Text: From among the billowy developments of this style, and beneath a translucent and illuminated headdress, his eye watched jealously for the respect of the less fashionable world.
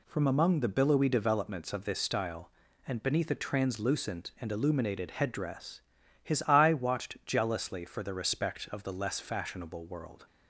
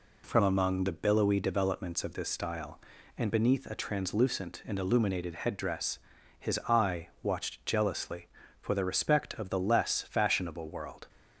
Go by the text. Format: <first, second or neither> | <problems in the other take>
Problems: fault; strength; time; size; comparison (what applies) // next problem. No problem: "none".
neither | none